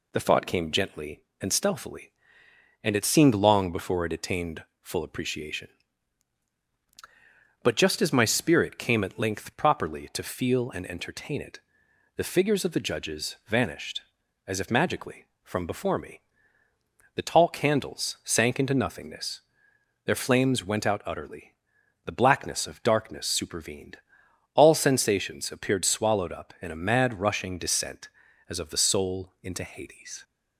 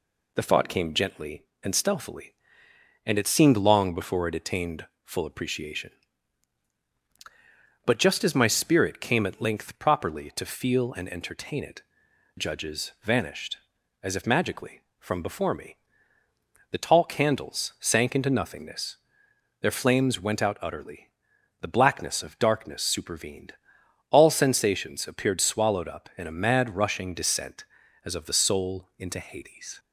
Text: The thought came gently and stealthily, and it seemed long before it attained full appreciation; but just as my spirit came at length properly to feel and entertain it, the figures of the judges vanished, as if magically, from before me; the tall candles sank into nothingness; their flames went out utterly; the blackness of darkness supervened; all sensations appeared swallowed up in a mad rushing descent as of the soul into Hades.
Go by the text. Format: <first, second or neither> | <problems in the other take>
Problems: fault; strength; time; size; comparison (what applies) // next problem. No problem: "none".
first | pauses between "attained" and "full"; slight; at 4.8 s; 0.18 s long; slight in the first // skips "the figures of the"; at 12.0 s